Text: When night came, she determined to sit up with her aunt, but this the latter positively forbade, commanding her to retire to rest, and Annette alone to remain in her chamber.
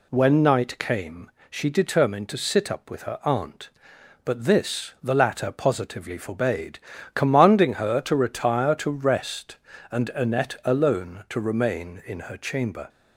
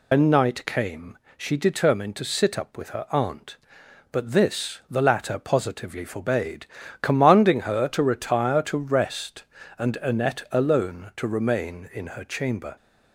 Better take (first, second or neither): first